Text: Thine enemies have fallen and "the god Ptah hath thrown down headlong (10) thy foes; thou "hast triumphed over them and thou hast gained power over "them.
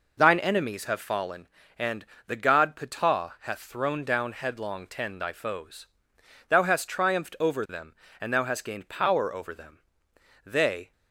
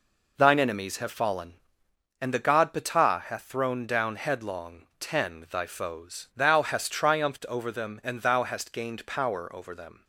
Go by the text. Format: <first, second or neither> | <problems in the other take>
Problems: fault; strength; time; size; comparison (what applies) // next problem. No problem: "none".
second | pauses between "and" and "the"; slight; at 2.0 s; 0.22 s long // goes on to say "They"; slight; from 10.4 s on; 0.46 s long